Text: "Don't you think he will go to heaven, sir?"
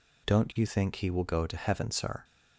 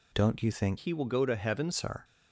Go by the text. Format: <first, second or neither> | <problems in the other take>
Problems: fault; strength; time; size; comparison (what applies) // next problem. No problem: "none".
first | changes voice from "he" to "heaven"; from 0.7 to 1.7 s; 1.0 s long